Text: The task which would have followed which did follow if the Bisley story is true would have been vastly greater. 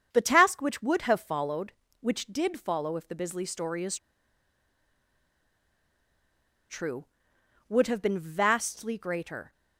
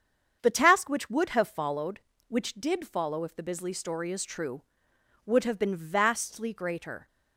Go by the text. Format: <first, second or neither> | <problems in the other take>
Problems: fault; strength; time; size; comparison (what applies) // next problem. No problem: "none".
second | starts louder than the rest; strong; until 1.1 s; 7.5 dB; strong in the second // pauses between "is" and "true"; strong; at 3.9 s; 2.7 s long